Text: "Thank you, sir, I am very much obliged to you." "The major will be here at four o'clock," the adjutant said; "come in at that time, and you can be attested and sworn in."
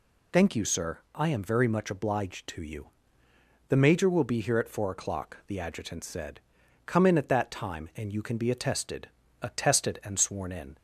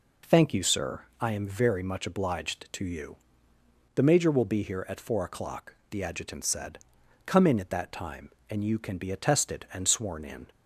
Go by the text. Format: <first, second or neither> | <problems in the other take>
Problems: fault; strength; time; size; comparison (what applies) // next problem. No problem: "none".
second | says "attested" twice; at 9.4 s